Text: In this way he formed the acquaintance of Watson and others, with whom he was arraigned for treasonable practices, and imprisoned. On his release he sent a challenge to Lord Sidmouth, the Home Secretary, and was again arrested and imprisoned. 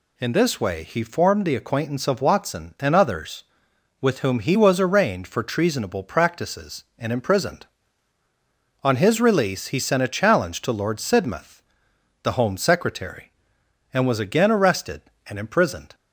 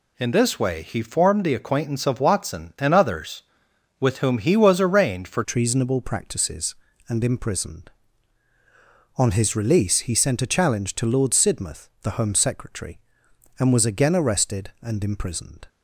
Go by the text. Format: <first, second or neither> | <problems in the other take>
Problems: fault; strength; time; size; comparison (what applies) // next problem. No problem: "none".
first | changes voice at "treasonable"; from 5.4 s on; 10.2 s long